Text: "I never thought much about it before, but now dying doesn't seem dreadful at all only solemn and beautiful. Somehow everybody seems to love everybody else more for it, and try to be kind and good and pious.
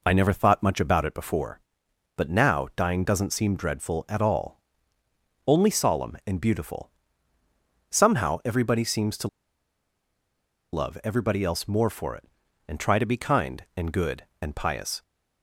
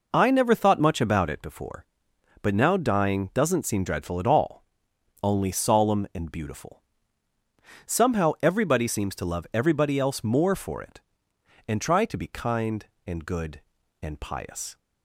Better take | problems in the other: second | pauses between "all" and "only"; noticeable; at 4.5 s; 0.86 s long; noticeable in the second // pauses between "to" and "love"; strong; at 9.2 s; 1.4 s long

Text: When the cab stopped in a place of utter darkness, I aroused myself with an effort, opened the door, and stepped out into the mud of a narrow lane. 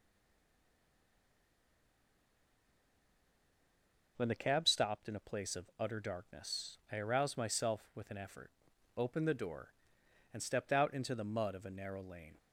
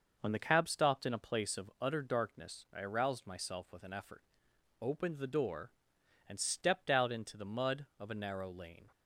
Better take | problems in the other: second | stays silent before the first word; strong; until 4.1 s; 4.1 s long

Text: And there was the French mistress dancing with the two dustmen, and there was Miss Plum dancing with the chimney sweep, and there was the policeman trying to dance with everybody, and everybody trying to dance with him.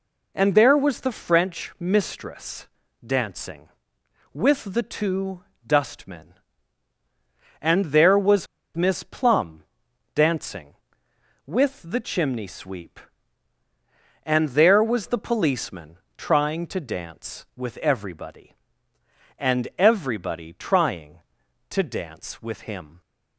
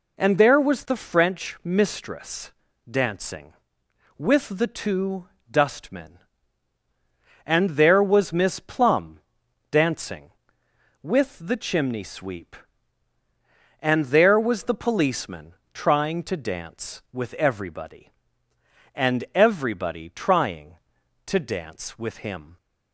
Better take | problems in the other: second | pauses between "mistress" and "dancing"; at 2.6 s; 0.38 s long; also in the second // pauses between "two" and "dustmen"; slight; at 5.4 s; 0.24 s long; slight in the second // pauses between "was" and "Miss"; slight; at 8.4 s; 0.30 s long // pauses between "Plum" and "dancing"; noticeable; at 9.6 s; 0.50 s long; noticeable in the second // pauses between "policeman" and "trying"; slight; at 15.9 s; 0.22 s long; slight in the second

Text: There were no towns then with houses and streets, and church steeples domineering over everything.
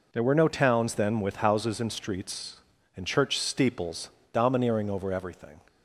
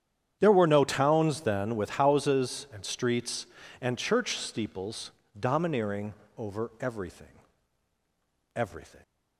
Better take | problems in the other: first | starts louder than the rest; strong; until 1.4 s; 9 dB // pauses between "steeples" and "domineering"; slight; at 5.1 s; 0.30 s long; slight in the first // pauses between "domineering" and "over"; slight; at 6.1 s; 0.22 s long // says "everything" twice; at 8.5 s

